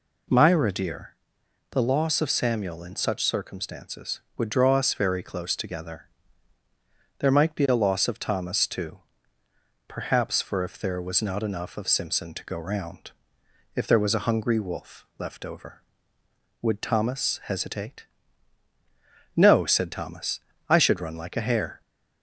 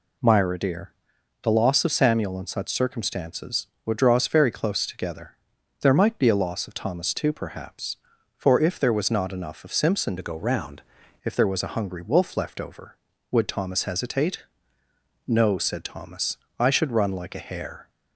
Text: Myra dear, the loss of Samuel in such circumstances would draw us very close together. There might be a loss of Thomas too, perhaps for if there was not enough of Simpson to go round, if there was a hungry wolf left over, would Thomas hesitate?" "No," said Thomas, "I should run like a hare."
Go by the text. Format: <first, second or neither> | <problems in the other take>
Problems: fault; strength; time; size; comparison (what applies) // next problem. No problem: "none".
first | changes voice from "to" to "round"; from 10.1 to 10.8 s; 0.7 s long